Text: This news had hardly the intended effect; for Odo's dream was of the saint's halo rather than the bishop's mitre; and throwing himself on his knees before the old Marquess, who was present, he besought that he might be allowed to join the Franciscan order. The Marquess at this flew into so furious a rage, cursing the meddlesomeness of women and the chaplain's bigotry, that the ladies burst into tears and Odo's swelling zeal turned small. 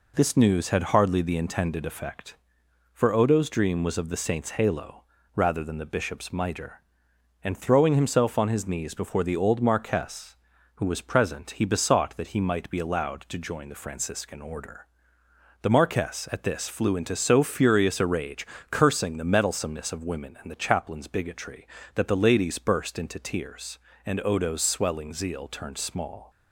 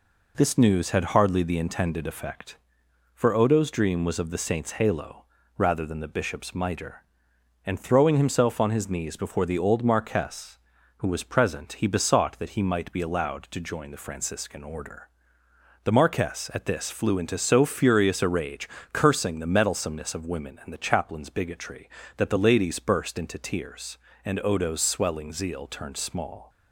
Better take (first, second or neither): neither